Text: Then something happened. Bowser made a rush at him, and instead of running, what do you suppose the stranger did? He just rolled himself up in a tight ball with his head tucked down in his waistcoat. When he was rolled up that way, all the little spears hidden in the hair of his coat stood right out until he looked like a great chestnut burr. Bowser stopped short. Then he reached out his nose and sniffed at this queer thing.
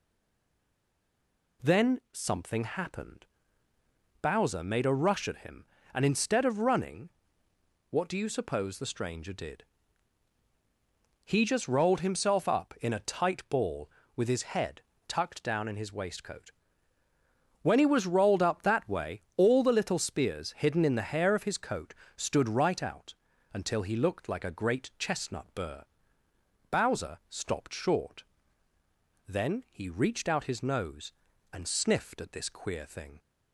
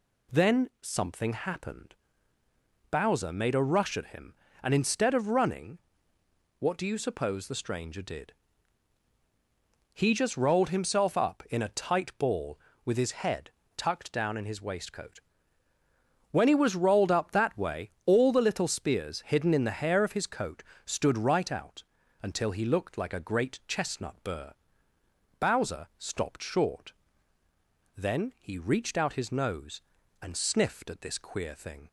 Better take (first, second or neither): second